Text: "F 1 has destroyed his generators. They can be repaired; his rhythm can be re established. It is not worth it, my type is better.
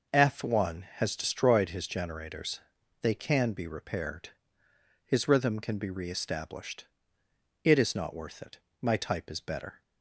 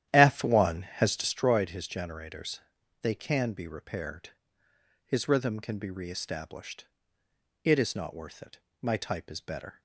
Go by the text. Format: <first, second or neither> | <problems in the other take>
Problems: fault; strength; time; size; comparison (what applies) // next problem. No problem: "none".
first | starts louder than the rest; strong; until 1.4 s; 11.5 dB